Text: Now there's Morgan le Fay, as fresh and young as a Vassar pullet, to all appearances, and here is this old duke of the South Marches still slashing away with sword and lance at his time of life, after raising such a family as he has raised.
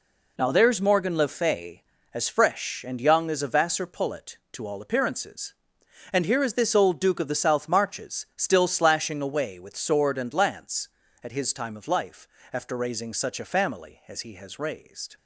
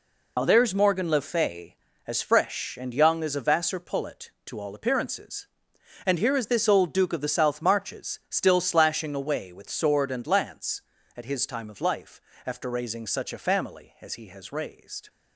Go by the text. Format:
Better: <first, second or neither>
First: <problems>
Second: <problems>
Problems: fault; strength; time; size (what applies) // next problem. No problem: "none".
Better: first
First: none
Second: loses the start of "Now"; at 0.3 s; 55 ms